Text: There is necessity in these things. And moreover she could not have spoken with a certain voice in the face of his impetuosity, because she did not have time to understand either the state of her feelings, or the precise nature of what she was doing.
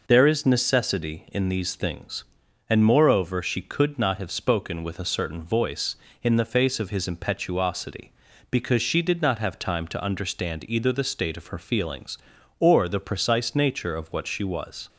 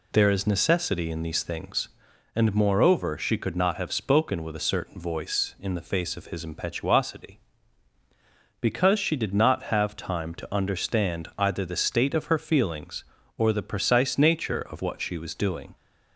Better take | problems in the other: second | stops before "doing"; at 14.8 s

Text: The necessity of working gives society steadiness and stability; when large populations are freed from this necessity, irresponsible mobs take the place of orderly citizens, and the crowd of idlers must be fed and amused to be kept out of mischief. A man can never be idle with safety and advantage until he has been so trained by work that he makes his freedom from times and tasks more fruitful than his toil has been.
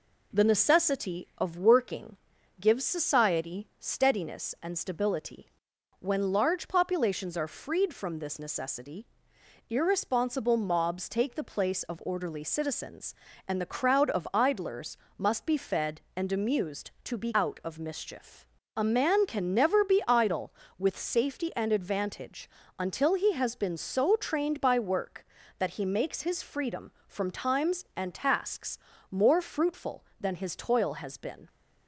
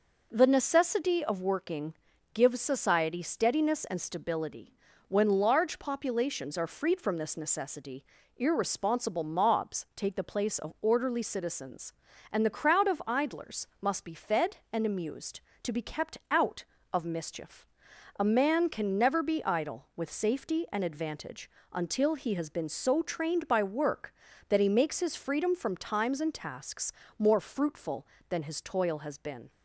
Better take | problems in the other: second | pauses between "working" and "gives"; at 2.1 s; 0.42 s long; also in the second // pauses between "idlers" and "must"; slight; at 14.9 s; 0.22 s long // skips "kept"; at 17.3 s // pauses between "advantage" and "until"; slight; at 22.4 s; 0.30 s long; slight in the second // pauses between "tasks" and "more"; slight; at 28.7 s; 0.32 s long; slight in the second

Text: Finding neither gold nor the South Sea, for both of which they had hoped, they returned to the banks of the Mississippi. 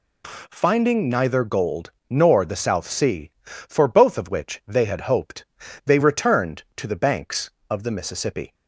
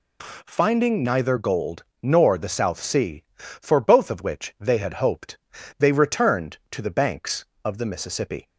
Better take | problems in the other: neither | pauses between "gold" and "nor"; slight; the same in both

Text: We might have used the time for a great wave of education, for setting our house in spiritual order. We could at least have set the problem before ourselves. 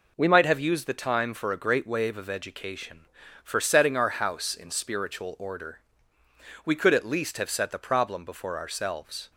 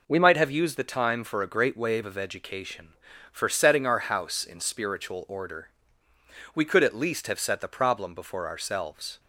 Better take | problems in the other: neither | none

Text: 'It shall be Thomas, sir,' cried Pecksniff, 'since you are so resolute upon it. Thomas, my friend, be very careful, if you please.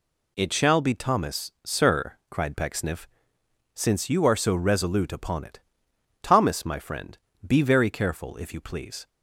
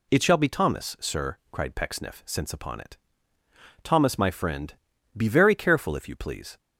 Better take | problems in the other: first | skips "you are so resolute"; at 2.5 s

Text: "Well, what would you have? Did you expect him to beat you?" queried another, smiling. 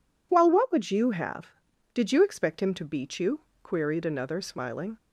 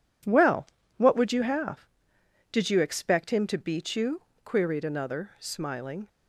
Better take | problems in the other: neither | none

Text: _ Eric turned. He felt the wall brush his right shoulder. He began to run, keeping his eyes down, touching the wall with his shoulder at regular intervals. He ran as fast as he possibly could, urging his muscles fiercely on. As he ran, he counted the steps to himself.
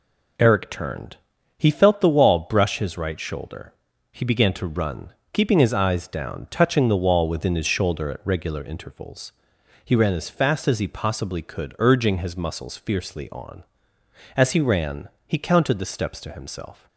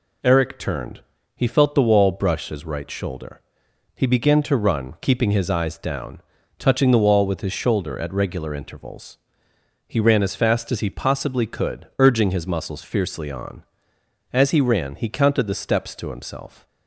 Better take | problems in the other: second | says "within" for "with"; at 7.2 s

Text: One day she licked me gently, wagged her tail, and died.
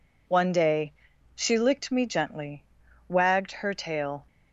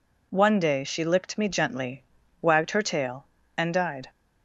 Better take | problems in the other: second | pauses between "day" and "she"; noticeable; at 0.9 s; 0.46 s long // stops before "and died"; at 4.2 s

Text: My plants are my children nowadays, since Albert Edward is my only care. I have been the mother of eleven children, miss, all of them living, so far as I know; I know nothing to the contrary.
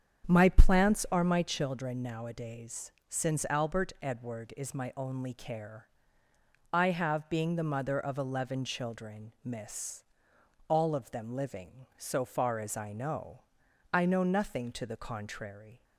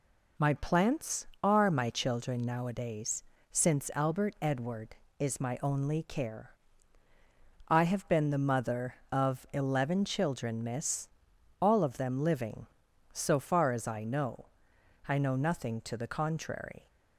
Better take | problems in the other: second | starts louder than the rest; until 1.3 s; 7 dB // says "being" for "been"; at 7.2 s

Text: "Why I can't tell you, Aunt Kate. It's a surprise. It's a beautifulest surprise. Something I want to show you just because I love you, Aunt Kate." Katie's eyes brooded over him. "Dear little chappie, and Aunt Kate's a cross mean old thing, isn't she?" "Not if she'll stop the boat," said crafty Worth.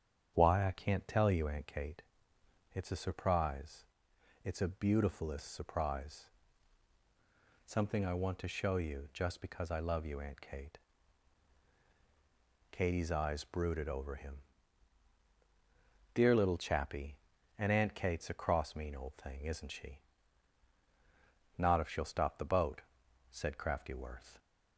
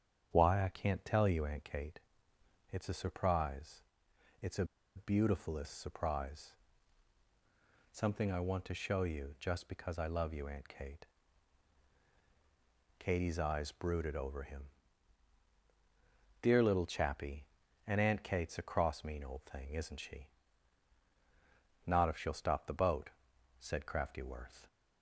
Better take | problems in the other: first | starts louder than the rest; strong; until 1.3 s; 8.5 dB; strong in the first // pauses between "a" and "beautifulest"; slight; at 4.6 s; 0.31 s long

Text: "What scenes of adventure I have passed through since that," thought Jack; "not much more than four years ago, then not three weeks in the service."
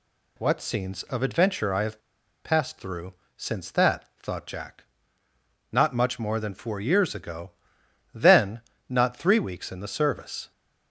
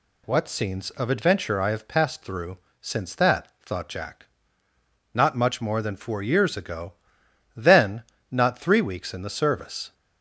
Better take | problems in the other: second | pauses between "have" and "passed"; at 2.0 s; 0.43 s long // pauses between "through" and "since"; slight; at 3.1 s; 0.22 s long; slight in the second // pauses between "then" and "not"; slight; at 8.6 s; 0.26 s long; slight in the second

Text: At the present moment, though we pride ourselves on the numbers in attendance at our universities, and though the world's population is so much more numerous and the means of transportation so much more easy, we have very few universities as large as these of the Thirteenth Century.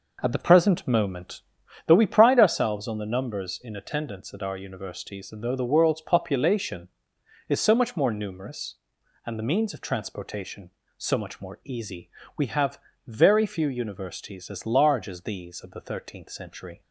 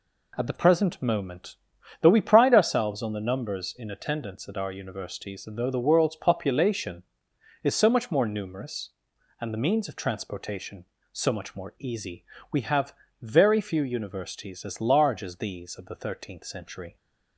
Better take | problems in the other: second | starts louder than the rest; noticeable; until 1.7 s; 5 dB // pauses between "have" and "very"; slight; at 12.7 s; 0.28 s long; slight in the second

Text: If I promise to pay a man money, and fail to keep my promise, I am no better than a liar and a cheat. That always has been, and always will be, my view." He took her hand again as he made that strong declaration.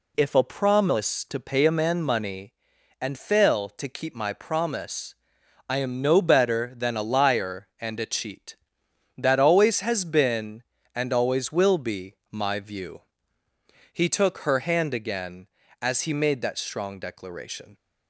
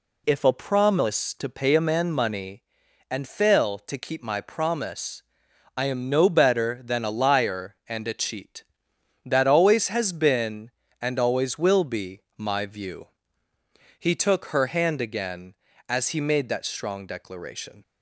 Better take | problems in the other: neither | none

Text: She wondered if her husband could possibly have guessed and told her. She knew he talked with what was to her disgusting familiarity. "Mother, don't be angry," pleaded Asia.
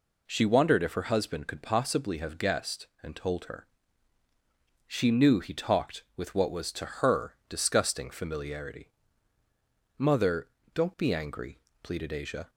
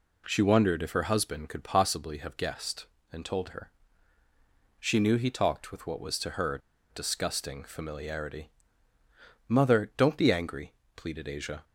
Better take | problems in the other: first | pauses between "her" and "disgusting"; slight; at 6.6 s; 0.33 s long

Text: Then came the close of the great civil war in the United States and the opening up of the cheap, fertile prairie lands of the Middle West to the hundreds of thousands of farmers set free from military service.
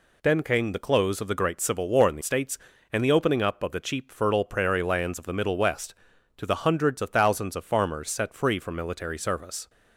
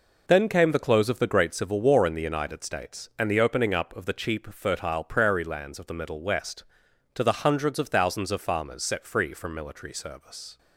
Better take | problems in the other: second | skips "United"; at 2.2 s

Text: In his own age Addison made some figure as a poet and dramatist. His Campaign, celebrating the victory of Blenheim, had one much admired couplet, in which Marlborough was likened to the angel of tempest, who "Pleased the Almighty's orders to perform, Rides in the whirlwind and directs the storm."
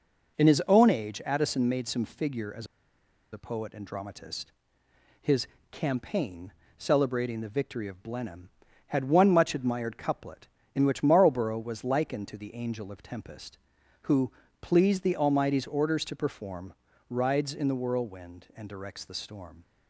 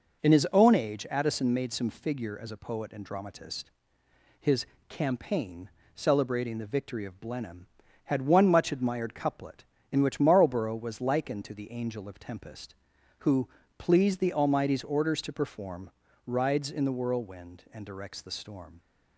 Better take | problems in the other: second | pauses between "as" and "a"; noticeable; at 2.6 s; 0.66 s long // pauses between "His" and "Campaign"; slight; at 5.4 s; 0.24 s long; slight in the second // pauses between "who" and "Pleased"; slight; at 14.3 s; 0.28 s long; slight in the second

